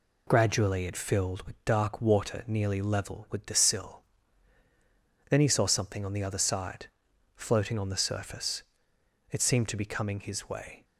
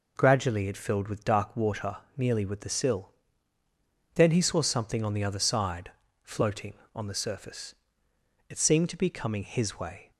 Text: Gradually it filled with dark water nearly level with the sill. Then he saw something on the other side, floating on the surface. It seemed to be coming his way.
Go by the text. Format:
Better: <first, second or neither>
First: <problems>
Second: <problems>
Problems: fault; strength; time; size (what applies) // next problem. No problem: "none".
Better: first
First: none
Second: pauses between "water" and "nearly"; slight; at 1.9 s; 0.20 s long // skips "level"; at 2.4 s